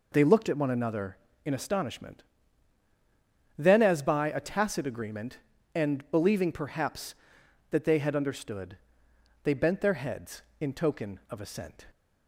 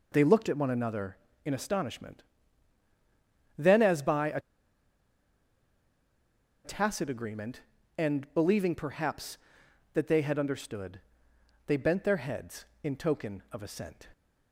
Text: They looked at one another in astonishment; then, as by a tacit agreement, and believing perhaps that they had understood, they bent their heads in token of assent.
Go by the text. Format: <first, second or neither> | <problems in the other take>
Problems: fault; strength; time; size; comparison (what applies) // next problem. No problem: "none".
first | pauses between "a" and "tacit"; strong; at 4.3 s; 2.2 s long